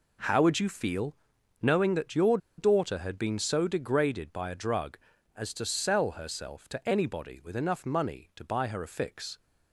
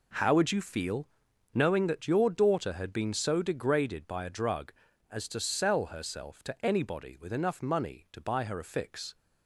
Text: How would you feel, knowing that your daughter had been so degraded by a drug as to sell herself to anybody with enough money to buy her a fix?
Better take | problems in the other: second | pauses between "your" and "daughter"; slight; at 2.3 s; 0.20 s long

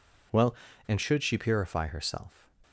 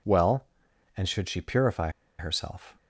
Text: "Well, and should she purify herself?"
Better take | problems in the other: first | pauses between "purify" and "herself"; slight; at 1.8 s; 0.29 s long

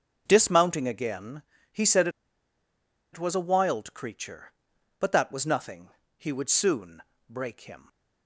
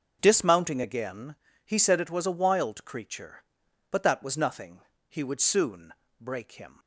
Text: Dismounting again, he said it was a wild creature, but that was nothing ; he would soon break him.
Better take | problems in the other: second | starts louder than the rest; until 1.2 s; 6.5 dB; also in the second // pauses between "said" and "it"; at 2.0 s; 1.0 s long // pauses between "soon" and "break"; slight; at 7.0 s; 0.26 s long; slight in the second

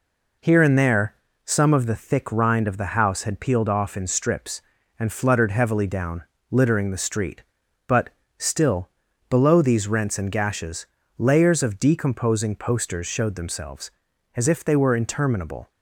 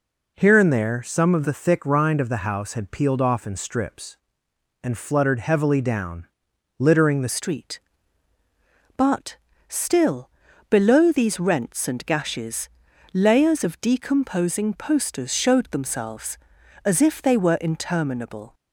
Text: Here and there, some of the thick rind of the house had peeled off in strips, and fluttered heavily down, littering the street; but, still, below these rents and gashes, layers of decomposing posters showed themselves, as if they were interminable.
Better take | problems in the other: first | changes voice at "street"; from 7.2 s on; 11.3 s long

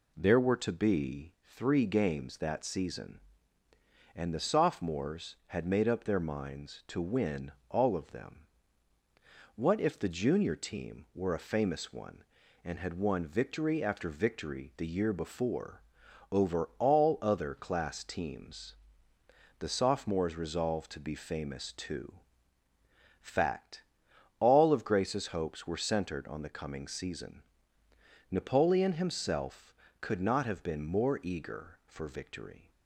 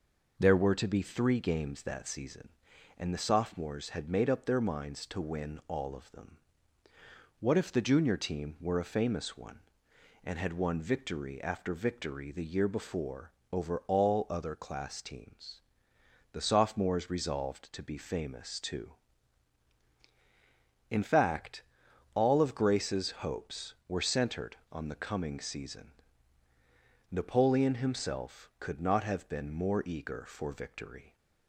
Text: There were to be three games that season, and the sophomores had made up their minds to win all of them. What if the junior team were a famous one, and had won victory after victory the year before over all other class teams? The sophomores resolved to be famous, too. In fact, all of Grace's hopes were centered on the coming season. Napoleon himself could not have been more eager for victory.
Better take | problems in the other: second | pauses between "win" and "all"; slight; at 7.5 s; 0.16 s long // pauses between "before" and "over"; noticeable; at 15.8 s; 0.50 s long; slight in the second // skips "In"; at 22.6 s

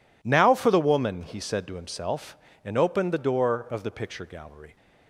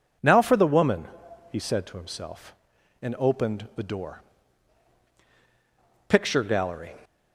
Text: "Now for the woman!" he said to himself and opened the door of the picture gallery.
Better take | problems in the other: first | skips "of the"; at 5.1 s

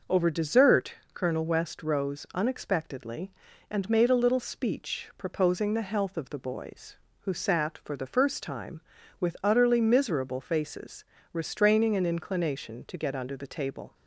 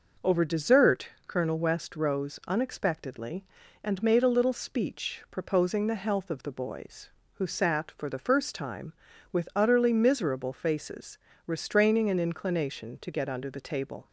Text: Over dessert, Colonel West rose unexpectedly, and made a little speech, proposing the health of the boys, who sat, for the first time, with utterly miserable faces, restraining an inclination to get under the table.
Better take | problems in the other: neither | none

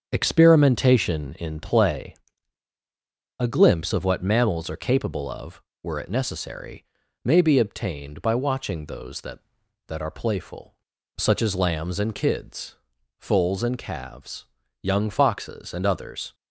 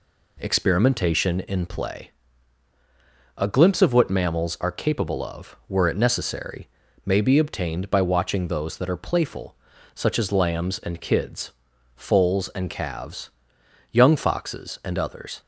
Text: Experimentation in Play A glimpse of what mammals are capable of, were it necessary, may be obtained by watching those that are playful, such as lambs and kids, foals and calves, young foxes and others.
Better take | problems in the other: second | starts louder than the rest; strong; until 1.1 s; 7.5 dB // pauses between "Play" and "A"; strong; at 2.1 s; 1.2 s long; strong in the second // says "that" twice; at 9.8 s

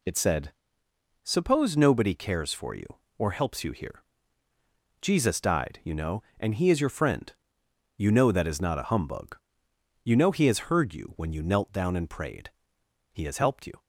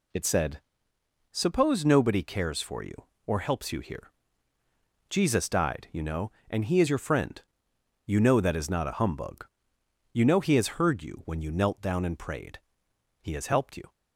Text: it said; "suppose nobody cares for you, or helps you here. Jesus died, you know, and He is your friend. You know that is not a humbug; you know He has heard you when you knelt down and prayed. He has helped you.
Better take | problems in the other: neither | none

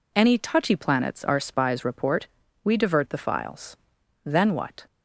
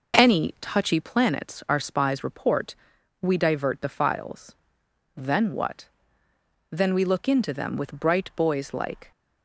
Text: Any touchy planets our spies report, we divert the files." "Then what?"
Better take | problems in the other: first | goes on to say "Then we look into them with bright boys like"; strong; from 6.7 s on; 2.4 s long

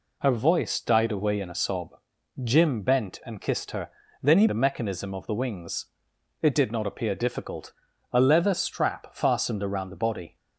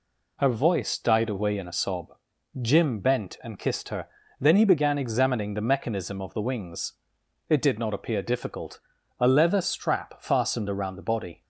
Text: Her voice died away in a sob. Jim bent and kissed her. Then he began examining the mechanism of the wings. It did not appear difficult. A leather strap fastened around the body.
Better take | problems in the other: second | skips "began examining"; at 4.4 s

